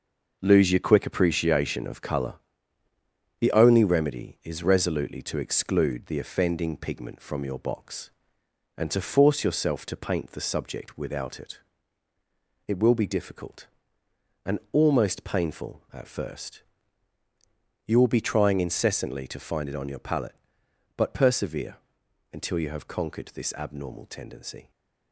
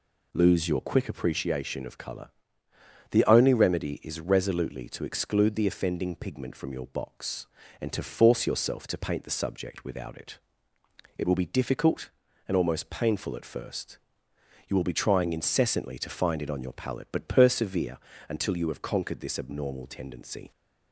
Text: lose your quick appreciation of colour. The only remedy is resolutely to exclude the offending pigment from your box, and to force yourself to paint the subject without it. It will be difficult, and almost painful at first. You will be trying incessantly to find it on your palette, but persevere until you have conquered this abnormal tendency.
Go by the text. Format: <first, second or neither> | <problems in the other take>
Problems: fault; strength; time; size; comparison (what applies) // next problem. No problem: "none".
second | gets quieter; throughout; 7 dB // pauses between "persevere" and "until"; noticeable; at 21.7 s; 0.56 s long; slight in the second